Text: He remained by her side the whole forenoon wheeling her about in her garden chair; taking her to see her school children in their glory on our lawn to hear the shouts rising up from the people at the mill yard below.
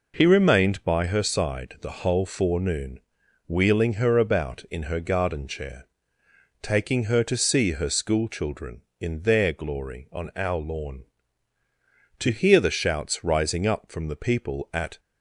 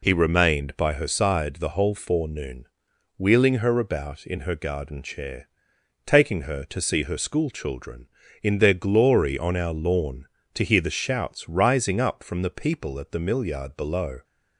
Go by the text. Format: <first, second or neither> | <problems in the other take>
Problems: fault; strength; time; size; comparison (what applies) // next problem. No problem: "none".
second | pauses between "forenoon" and "wheeling"; noticeable; at 3.0 s; 0.48 s long; noticeable in the second // stops before "the mill yard below"; at 14.9 s